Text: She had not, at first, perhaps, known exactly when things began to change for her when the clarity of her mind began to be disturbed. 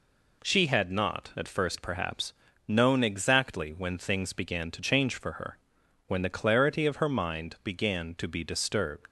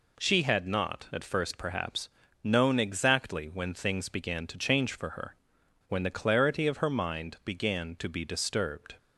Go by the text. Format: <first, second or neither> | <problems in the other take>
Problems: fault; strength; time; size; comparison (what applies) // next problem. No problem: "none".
second | pauses between "her" and "when"; noticeable; at 5.5 s; 0.52 s long; noticeable in the second // leaves "disturbed" unfinished; at 9.0 s; 85 ms